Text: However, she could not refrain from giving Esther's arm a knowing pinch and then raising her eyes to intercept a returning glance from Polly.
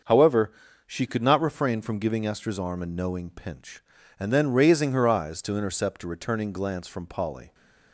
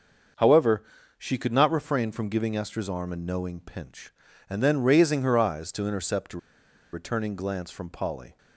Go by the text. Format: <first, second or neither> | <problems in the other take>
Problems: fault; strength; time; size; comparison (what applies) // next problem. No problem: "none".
first | starts louder than the rest; until 1.6 s; 6.5 dB; also in the first // pauses between "a" and "returning"; noticeable; at 6.3 s; 0.54 s long